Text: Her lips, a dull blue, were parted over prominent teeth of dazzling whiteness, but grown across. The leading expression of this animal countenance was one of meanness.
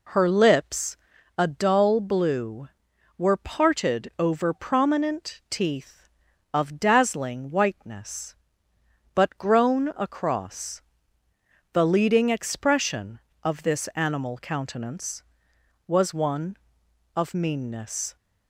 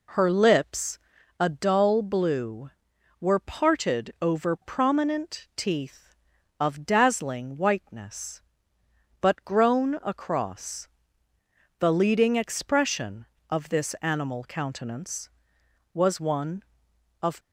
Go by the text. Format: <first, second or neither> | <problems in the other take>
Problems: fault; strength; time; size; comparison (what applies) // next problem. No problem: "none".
first | stops before "meanness"; at 17.4 s